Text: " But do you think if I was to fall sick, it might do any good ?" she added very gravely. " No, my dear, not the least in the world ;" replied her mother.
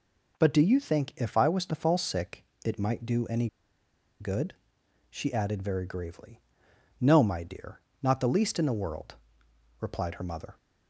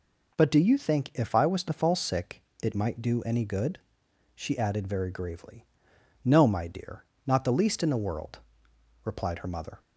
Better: second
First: pauses between "any" and "good"; noticeable; at 3.4 s; 0.72 s long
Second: none

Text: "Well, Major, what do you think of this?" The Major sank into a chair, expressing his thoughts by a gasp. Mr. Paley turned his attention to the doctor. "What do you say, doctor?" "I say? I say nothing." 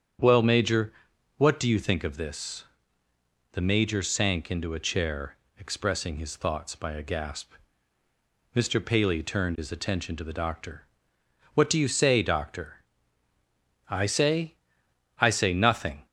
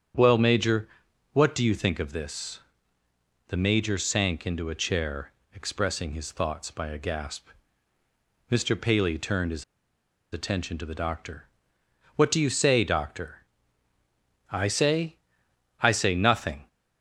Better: first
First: starts louder than the rest; strong; until 1.6 s; 8 dB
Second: starts louder than the rest; strong; until 1.6 s; 8 dB // pauses between "his" and "attention"; noticeable; at 9.6 s; 0.69 s long

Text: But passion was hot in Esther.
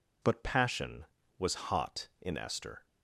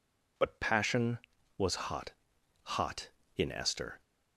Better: first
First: none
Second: says "hot" twice; at 2.6 s

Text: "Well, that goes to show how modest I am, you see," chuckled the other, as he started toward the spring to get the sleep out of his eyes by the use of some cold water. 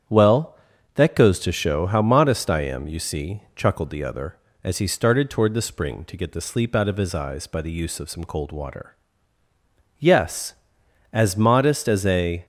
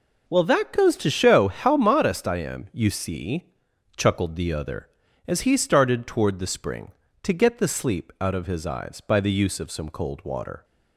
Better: second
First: starts louder than the rest; strong; until 1.4 s; 8.5 dB // goes on to say "Yes as modest as a"; strong; from 9.9 s on; 2.4 s long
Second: none

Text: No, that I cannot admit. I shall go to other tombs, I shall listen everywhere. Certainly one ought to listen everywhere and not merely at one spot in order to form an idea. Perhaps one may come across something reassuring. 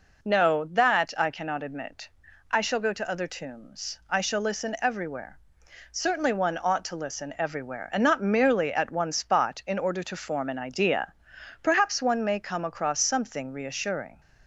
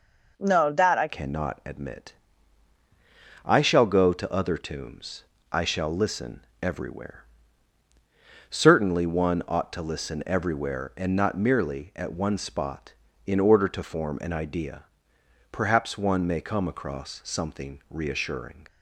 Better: first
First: none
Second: changes voice at "cannot"; from 1.0 s on; 17.6 s long // pauses between "listen" and "everywhere"; slight; at 6.4 s; 0.22 s long

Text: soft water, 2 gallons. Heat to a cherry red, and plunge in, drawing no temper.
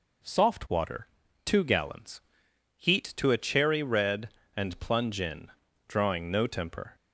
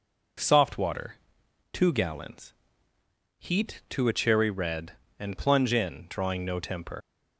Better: first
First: none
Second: leaves "temper" unfinished; at 7.0 s; 75 ms

